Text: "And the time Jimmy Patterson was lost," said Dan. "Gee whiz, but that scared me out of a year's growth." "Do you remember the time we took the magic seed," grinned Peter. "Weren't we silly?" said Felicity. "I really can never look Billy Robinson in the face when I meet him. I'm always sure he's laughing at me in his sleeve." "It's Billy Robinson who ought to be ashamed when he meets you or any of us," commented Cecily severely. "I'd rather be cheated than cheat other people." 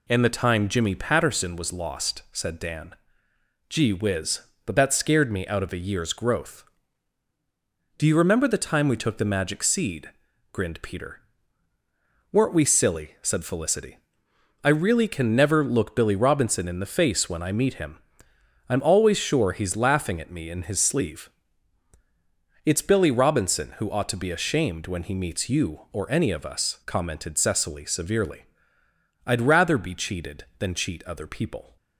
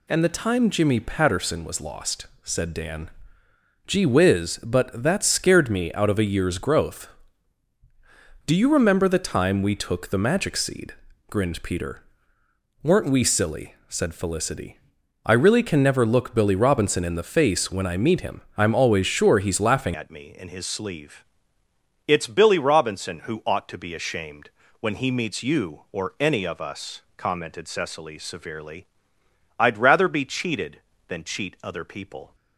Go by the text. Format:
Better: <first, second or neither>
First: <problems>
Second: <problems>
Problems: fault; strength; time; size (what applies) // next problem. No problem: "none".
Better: first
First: none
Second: changes voice at "at"; from 19.9 s on; 12.4 s long // pauses between "ashamed" and "when"; slight; at 24.5 s; 0.28 s long